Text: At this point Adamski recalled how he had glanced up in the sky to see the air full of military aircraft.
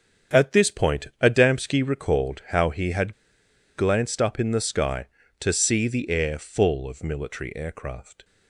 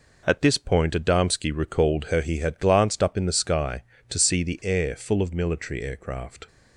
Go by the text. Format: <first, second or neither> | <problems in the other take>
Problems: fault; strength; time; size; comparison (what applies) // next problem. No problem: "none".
second | starts louder than the rest; strong; until 1.4 s; 7.5 dB // pauses between "had" and "glanced"; noticeable; at 3.1 s; 0.64 s long